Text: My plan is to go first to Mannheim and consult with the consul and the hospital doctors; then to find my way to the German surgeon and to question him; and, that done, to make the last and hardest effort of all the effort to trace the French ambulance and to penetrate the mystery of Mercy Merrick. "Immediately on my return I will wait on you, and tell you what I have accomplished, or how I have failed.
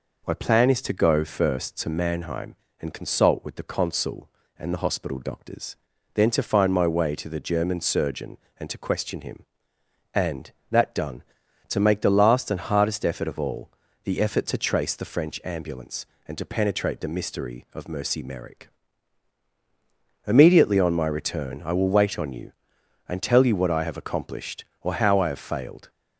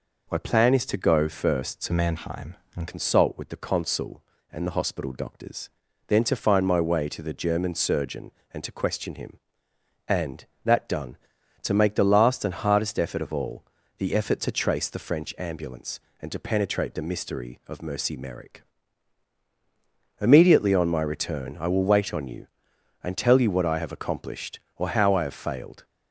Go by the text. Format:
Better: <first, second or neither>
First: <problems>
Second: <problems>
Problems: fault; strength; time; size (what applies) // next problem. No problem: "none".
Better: first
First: pauses between "all" and "the"; slight; at 13.6 s; 0.36 s long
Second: changes voice from "Mannheim" to "and"; from 1.9 to 2.8 s; 0.9 s long // pauses between "all" and "the"; slight; at 13.6 s; 0.36 s long